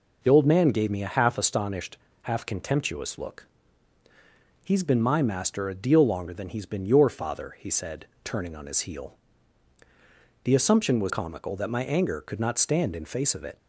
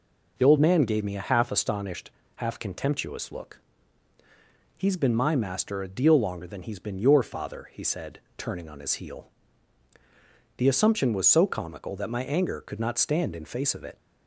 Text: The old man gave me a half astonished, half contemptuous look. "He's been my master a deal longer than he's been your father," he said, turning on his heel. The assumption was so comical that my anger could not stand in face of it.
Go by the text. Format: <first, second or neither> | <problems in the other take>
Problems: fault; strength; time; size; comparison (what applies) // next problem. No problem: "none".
second | skips "so"; at 11.0 s